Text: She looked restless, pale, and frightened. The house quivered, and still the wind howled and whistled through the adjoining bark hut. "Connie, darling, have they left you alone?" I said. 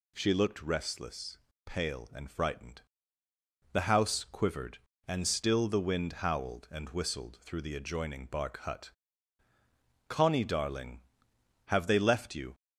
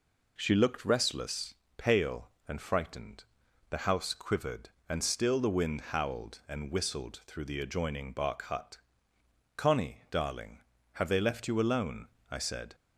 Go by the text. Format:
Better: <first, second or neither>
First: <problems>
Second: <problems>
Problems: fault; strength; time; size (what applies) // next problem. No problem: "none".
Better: second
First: stops before "alone I said"; at 12.5 s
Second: none